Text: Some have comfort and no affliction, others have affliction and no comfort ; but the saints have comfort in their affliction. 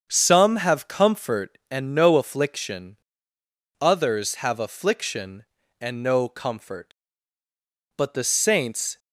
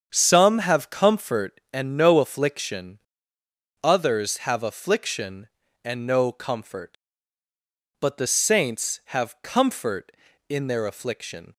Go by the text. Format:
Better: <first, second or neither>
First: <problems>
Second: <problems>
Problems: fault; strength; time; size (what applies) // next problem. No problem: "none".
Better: second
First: starts louder than the rest; strong; until 1.1 s; 7.5 dB // stops before "have comfort in their affliction"; at 8.9 s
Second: starts louder than the rest; strong; until 1.1 s; 7.5 dB